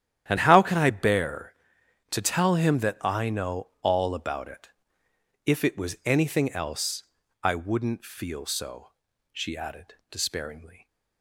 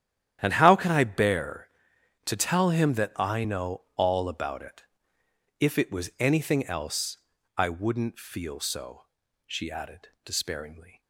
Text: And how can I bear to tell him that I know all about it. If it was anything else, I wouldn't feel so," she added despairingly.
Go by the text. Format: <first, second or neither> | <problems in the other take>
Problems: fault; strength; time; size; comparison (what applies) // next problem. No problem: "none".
neither | starts louder than the rest; strong; the same in both // pauses between "added" and "despairingly"; slight; the same in both